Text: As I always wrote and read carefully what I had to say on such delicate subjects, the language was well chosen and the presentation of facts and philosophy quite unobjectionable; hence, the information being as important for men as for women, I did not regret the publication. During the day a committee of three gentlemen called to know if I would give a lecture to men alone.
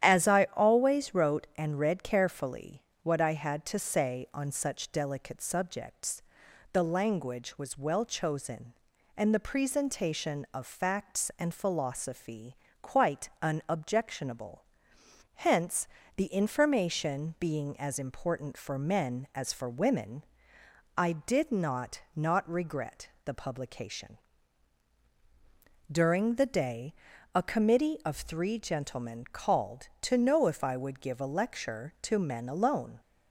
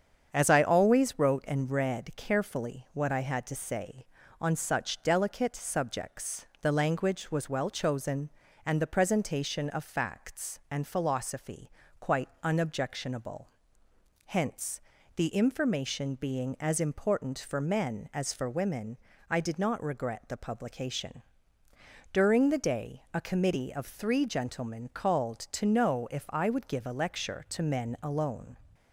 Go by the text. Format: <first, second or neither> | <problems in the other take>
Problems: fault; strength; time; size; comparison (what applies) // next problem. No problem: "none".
second | starts louder than the rest; strong; until 1.1 s; 10 dB; strong in the second // pauses between "carefully" and "what"; slight; at 2.8 s; 0.20 s long // pauses between "philosophy" and "quite"; slight; at 12.5 s; 0.24 s long; slight in the second // says "not" twice; at 22.1 s // pauses between "regret" and "the"; slight; at 23.0 s; 0.16 s long // pauses between "day" and "a"; at 26.9 s; 0.42 s long